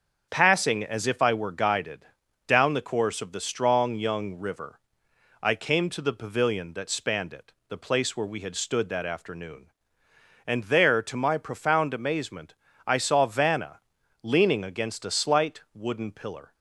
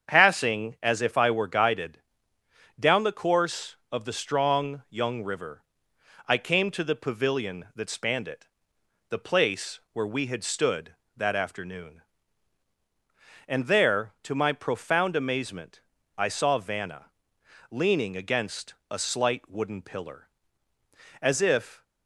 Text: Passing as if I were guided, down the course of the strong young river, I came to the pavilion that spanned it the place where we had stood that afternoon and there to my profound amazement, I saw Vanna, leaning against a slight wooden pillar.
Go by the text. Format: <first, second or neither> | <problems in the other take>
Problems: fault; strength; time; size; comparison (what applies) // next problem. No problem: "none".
first | starts louder than the rest; strong; until 1.1 s; 7 dB; also in the first // pauses between "it" and "the"; noticeable; at 8.4 s; 0.64 s long; slight in the first // pauses between "against" and "a"; slight; at 18.7 s; 0.18 s long // goes on to say "As if"; noticeable; from 21.2 s on; 0.62 s long